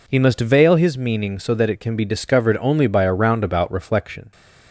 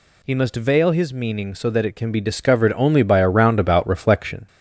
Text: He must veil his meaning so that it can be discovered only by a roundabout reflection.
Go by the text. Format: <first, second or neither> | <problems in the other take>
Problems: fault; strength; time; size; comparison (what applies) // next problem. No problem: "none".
first | gets louder; slight; throughout; 3 dB